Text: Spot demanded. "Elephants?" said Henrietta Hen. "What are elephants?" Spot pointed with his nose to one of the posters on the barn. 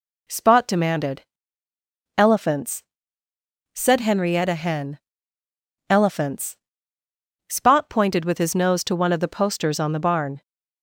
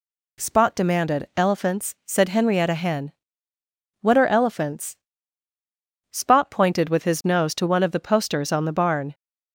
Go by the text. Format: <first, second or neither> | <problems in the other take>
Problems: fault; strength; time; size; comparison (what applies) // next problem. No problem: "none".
second | skips "What are"; at 5.4 s